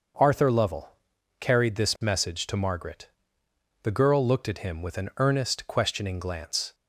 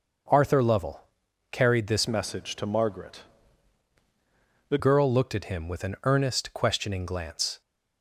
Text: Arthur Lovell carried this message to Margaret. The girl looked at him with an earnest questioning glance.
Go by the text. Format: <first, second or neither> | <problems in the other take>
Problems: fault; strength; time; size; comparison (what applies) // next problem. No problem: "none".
first | starts louder than the rest; until 1.7 s; 6.5 dB; also in the first // pauses between "Lovell" and "carried"; noticeable; at 1.0 s; 0.50 s long; noticeable in the first // changes voice from "message" to "The"; from 2.0 to 4.7 s; 2.7 s long